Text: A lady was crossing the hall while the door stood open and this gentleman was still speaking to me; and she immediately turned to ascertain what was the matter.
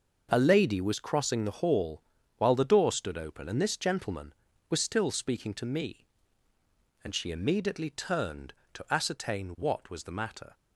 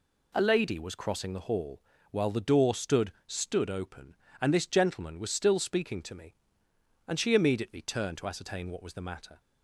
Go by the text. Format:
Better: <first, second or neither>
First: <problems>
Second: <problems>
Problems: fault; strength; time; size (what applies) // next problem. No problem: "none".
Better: first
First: pauses between "hall" and "while"; slight; at 2.0 s; 0.34 s long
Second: pauses between "hall" and "while"; slight; at 1.8 s; 0.28 s long // says "stood" twice; at 3.2 s